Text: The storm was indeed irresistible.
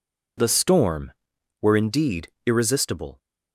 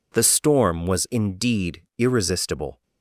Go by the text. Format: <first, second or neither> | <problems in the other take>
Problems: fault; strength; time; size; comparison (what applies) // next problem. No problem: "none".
second | says "were" for "was"; at 1.6 s // pauses between "indeed" and "irresistible"; slight; at 2.2 s; 0.18 s long